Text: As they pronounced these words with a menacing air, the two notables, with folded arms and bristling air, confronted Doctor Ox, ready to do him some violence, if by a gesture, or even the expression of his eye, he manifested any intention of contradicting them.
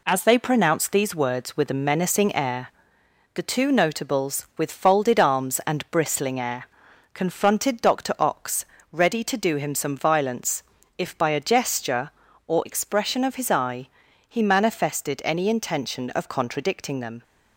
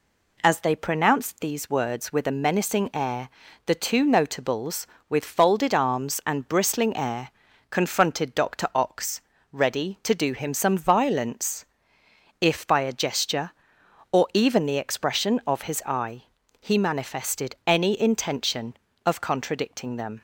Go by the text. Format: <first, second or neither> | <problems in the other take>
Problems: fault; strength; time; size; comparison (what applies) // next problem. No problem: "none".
second | skips "even the"; at 12.6 s